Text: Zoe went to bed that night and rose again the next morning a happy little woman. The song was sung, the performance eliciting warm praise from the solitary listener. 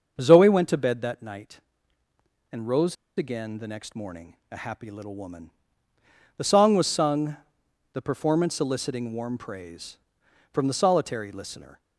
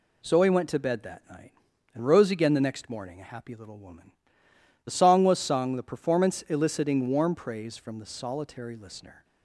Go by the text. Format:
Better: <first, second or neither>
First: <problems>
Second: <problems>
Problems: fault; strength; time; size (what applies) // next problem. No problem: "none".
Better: second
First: starts louder than the rest; until 1.2 s; 6.5 dB // pauses between "rose" and "again"; slight; at 2.9 s; 0.22 s long // pauses between "morning" and "a"; slight; at 4.3 s; 0.16 s long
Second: none